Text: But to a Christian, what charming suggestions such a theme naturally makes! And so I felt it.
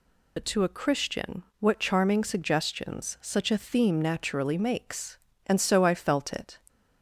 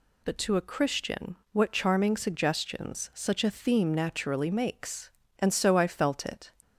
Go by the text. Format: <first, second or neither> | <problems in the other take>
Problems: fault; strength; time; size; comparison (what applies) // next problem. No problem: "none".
second | loses the start of "But"; at 0.3 s; 45 ms